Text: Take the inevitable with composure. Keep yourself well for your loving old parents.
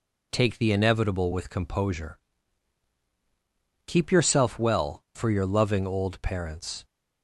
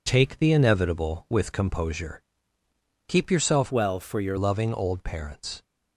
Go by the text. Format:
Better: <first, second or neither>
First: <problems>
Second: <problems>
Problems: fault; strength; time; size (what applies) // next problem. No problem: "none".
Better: first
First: none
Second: changes voice from "well" to "your"; from 3.7 to 4.3 s; 0.6 s long